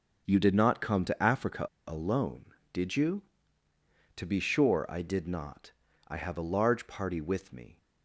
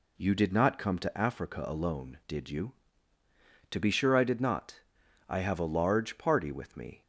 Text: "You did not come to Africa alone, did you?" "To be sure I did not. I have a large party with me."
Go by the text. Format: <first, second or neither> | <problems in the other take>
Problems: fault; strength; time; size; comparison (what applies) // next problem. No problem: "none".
second | pauses between "Africa" and "alone"; slight; at 1.6 s; 0.20 s long